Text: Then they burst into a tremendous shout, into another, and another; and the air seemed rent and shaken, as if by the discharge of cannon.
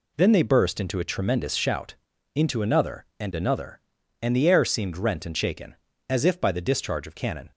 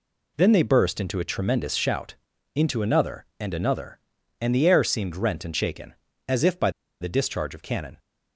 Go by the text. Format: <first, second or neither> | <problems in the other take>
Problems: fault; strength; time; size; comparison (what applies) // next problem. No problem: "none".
first | pauses between "by" and "the"; slight; at 6.6 s; 0.31 s long